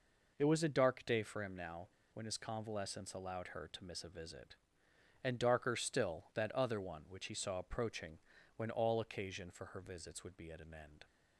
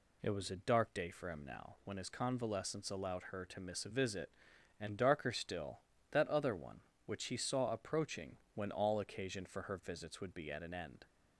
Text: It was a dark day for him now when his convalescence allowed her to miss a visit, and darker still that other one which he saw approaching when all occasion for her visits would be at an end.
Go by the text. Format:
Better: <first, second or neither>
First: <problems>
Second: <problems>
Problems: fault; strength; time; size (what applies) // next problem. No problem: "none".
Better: second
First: pauses between "now" and "when"; slight; at 1.8 s; 0.25 s long // pauses between "approaching" and "when"; slight; at 8.1 s; 0.36 s long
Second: pauses between "approaching" and "when"; slight; at 8.3 s; 0.16 s long